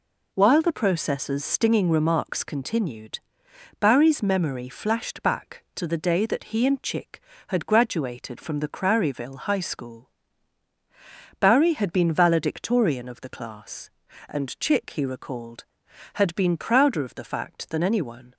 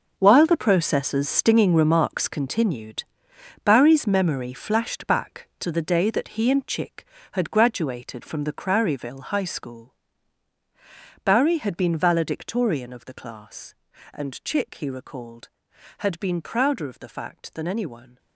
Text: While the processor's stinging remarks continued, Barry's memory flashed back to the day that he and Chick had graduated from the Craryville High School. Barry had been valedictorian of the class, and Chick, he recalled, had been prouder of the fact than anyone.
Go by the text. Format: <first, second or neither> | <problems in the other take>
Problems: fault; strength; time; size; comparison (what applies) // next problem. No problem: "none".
first | gets quieter; strong; throughout; 12.5 dB